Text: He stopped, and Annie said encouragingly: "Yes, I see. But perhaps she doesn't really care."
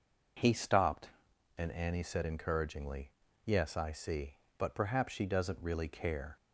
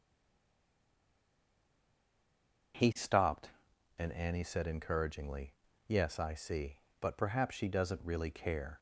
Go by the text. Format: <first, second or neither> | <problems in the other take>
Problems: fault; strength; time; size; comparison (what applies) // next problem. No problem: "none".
first | stays silent before the first word; strong; until 2.7 s; 2.7 s long